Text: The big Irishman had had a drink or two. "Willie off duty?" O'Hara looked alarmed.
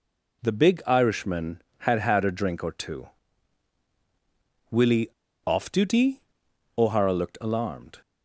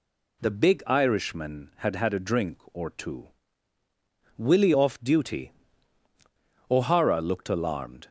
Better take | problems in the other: second | pauses between "Willie" and "off"; at 5.0 s; 0.37 s long

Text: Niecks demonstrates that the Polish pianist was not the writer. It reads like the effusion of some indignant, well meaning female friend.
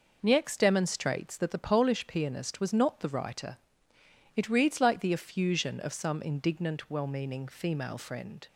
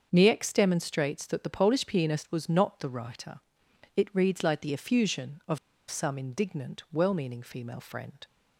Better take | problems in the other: first | starts louder than the rest; until 1.1 s; 6.5 dB // pauses between "of" and "some"; slight; at 5.5 s; 0.32 s long

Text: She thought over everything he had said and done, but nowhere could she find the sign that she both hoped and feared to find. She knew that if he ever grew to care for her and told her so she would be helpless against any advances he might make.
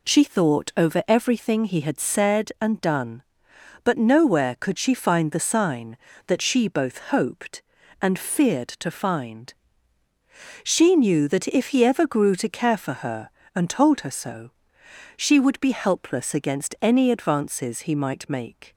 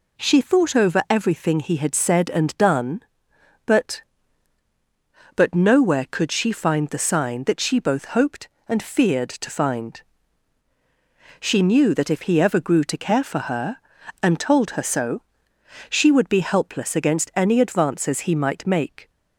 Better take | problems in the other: first | says "but" twice; at 5.3 s // pauses between "so" and "she"; noticeable; at 15.2 s; 0.68 s long; noticeable in the first

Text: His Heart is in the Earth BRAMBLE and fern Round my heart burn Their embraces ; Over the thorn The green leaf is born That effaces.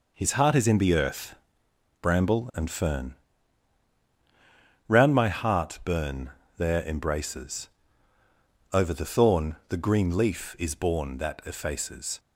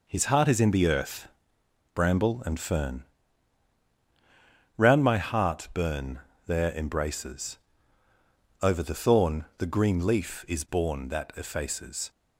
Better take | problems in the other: neither | pauses between "Earth" and "BRAMBLE"; noticeable; the same in both // pauses between "fern" and "Round"; strong; the same in both // pauses between "burn" and "Their"; slight; the same in both

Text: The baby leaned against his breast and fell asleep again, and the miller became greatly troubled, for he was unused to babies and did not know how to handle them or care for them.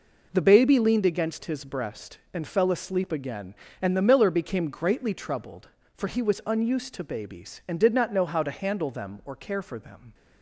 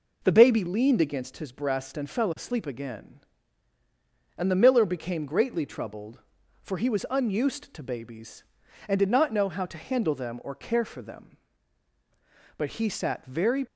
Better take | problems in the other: first | goes on to say "But he sat very"; noticeable; from 12.5 s on; 1.0 s long

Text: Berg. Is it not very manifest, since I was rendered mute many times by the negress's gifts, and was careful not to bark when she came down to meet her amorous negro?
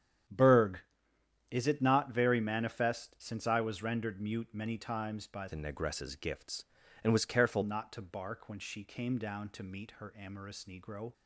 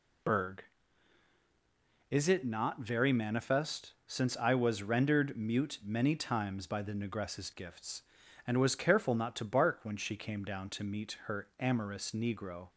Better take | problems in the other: second | starts louder than the rest; strong; until 1.9 s; 10 dB // changes voice from "the" to "careful"; from 5.4 to 7.6 s; 2.2 s long

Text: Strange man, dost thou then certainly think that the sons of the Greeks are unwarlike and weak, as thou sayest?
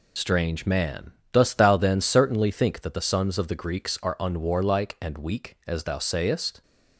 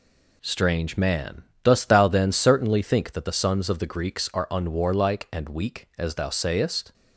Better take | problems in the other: second | loses the start of "Strange"; at 0.1 s; 60 ms

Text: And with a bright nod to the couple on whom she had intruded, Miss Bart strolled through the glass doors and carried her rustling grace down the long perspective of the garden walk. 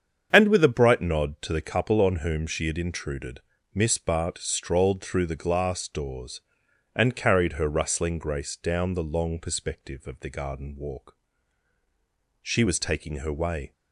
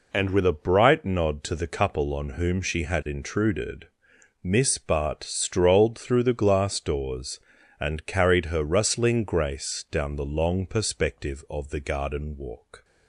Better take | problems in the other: second | starts louder than the rest; strong; until 1.3 s; 7.5 dB // goes on to say "She was taking her way"; noticeable; from 12.4 s on; 1.3 s long

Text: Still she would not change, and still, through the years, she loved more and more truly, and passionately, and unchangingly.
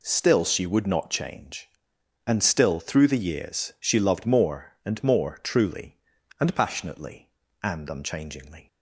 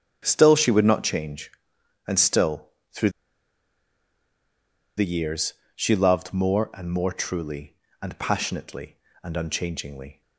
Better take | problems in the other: first | starts louder than the rest; strong; until 1.2 s; 9.5 dB // pauses between "through" and "the"; strong; at 3.0 s; 1.8 s long

